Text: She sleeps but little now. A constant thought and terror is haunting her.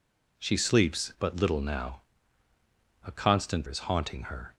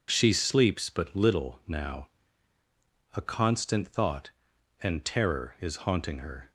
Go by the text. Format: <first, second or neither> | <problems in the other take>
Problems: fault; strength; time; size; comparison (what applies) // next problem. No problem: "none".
second | skips "thought and terror"; at 3.6 s